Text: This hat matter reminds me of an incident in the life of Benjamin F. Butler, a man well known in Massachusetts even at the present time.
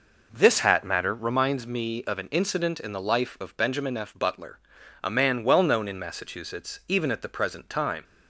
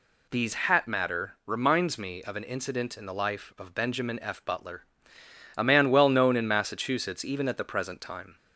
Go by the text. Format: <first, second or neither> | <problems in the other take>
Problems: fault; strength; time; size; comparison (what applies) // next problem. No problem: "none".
first | says "These" for "This"; at 0.2 s